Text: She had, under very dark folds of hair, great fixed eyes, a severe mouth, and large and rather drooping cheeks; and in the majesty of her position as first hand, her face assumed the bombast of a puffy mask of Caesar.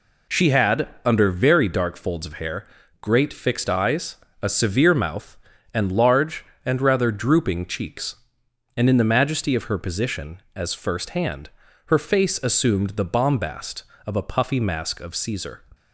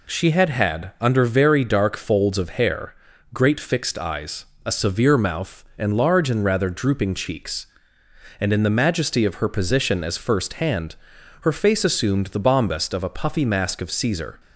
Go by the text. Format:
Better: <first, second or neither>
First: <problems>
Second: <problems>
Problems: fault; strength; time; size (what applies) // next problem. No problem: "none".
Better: first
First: none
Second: says "had" twice; at 0.4 s